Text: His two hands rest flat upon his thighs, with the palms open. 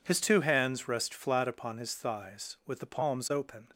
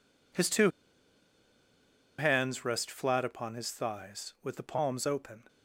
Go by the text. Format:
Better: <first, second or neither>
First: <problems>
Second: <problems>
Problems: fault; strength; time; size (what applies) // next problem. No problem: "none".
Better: first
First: none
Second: pauses between "two" and "hands"; strong; at 0.7 s; 1.4 s long